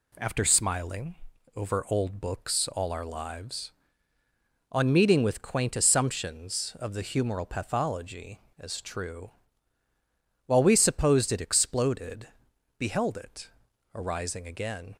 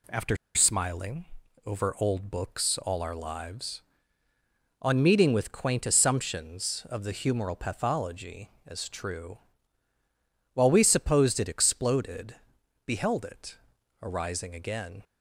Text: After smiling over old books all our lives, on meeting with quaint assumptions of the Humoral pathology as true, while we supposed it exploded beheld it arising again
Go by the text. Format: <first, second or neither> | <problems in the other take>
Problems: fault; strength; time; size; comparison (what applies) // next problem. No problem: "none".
first | pauses between "After" and "smiling"; slight; at 0.3 s; 0.18 s long // pauses between "smiling" and "over"; at 1.2 s; 0.40 s long; also in the first // pauses between "exploded" and "beheld"; noticeable; at 12.3 s; 0.50 s long; noticeable in the first // pauses between "it" and "arising"; noticeable; at 13.5 s; 0.46 s long; noticeable in the first